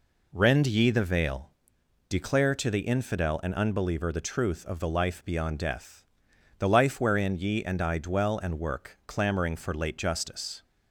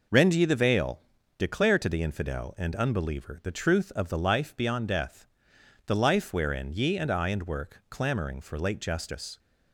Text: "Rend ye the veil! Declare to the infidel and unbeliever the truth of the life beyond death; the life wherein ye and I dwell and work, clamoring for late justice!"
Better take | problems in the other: first | skips "dwell"; at 7.2 s

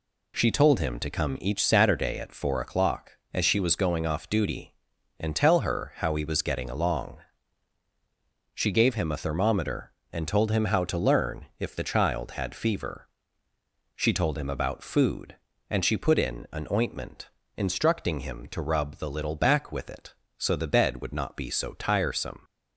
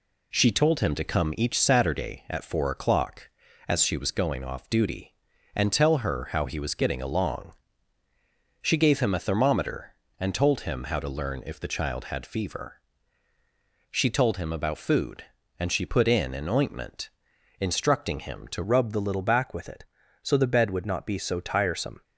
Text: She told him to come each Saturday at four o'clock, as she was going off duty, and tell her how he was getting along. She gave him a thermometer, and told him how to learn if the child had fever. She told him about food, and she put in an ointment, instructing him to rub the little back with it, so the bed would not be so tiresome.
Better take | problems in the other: first | changes voice at "rub"; from 18.6 s on; 3.4 s long

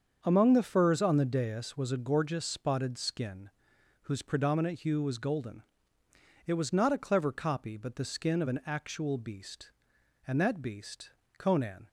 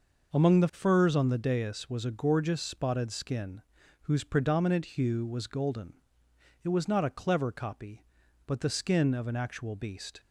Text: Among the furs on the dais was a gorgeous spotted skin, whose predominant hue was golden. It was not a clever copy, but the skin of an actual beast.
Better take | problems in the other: second | starts louder than the rest; until 1.2 s; 7 dB // goes on to say "And that beast Conan"; from 10.2 s on; 1.6 s long

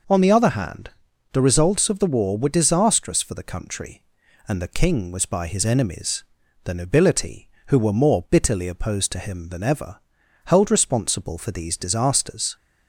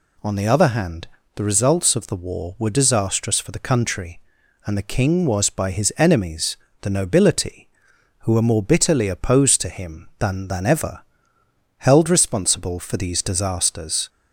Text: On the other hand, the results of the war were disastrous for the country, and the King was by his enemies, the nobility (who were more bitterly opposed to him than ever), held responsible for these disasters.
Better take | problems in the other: first | says "than" twice; at 10.4 s

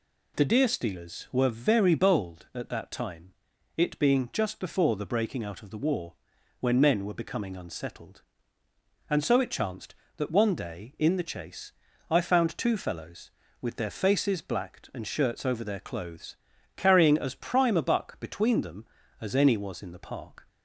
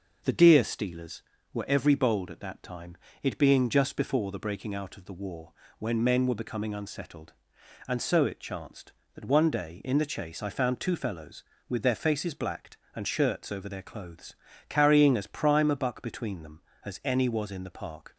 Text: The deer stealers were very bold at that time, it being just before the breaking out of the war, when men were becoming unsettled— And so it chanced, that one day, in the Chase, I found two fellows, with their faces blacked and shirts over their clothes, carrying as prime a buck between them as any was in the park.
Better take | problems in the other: first | starts louder than the rest; noticeable; until 1.5 s; 6 dB // says "every" for "very"; at 1.6 s

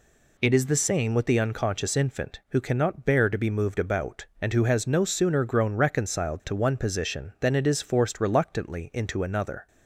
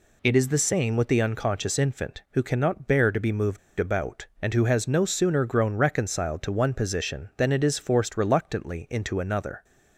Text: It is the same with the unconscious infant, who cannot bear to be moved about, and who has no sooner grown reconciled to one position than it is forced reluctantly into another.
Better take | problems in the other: first | pauses between "moved" and "about"; slight; at 3.5 s; 0.20 s long

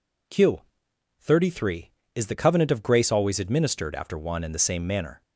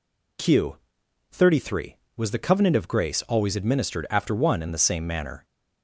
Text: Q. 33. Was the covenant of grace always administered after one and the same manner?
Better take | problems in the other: second | says "Is" for "Was"; at 2.1 s

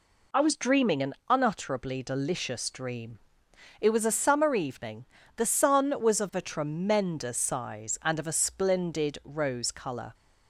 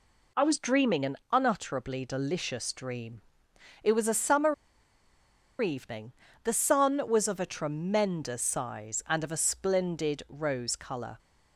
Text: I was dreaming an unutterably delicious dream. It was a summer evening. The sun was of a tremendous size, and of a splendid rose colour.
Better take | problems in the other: first | pauses between "an" and "unutterably"; slight; at 1.1 s; 0.16 s long; slight in the first // pauses between "summer" and "evening"; at 4.5 s; 1.0 s long

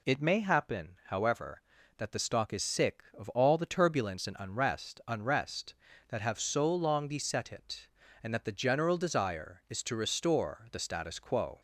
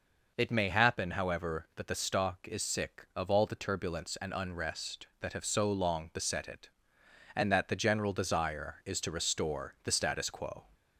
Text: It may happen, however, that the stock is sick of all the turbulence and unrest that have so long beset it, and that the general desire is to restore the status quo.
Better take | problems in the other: second | says "unrest" twice; at 5.0 s

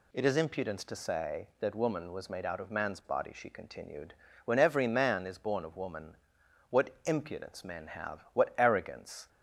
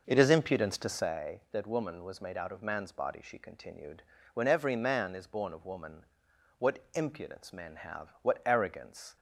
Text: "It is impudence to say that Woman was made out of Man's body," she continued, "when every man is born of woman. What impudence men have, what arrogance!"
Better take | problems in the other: first | starts louder than the rest; noticeable; until 1.1 s; 5.5 dB

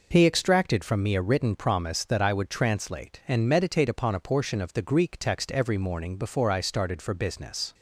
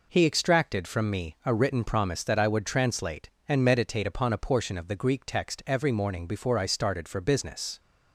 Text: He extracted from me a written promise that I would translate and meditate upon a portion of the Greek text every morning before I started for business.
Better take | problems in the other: neither | none

